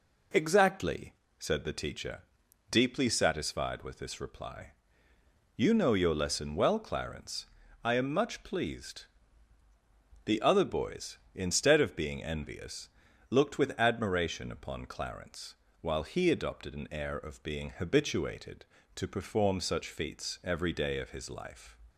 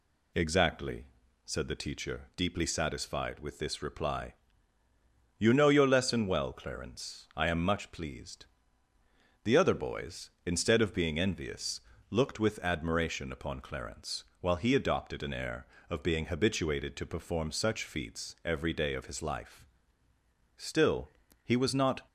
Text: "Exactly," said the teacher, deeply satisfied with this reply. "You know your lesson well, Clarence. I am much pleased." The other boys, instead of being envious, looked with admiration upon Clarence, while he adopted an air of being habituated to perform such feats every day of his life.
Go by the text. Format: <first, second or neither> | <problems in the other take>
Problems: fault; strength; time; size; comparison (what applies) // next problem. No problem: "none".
first | goes on to say "Still he was not"; from 20.6 s on; 1.4 s long